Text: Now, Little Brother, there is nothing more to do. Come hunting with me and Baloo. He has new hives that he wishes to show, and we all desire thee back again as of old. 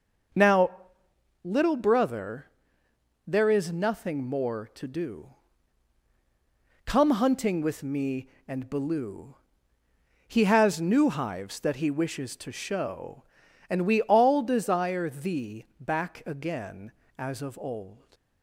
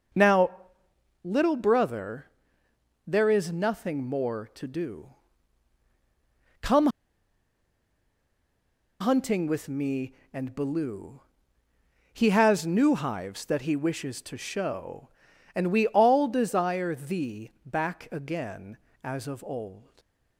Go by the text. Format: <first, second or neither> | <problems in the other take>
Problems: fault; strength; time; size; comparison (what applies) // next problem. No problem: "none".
first | starts louder than the rest; until 1.8 s; 6 dB; noticeable in the first // pauses between "Come" and "hunting"; strong; at 6.8 s; 2.1 s long